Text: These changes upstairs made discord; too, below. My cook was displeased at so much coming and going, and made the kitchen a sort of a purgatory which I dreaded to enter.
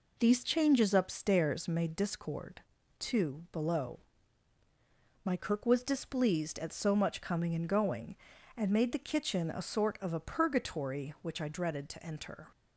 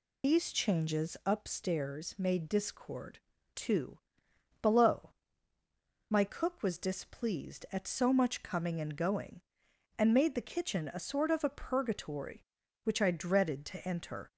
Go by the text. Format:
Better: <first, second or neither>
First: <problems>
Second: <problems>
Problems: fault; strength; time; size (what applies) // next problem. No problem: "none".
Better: first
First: none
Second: loses the start of "These"; at 0.2 s; 50 ms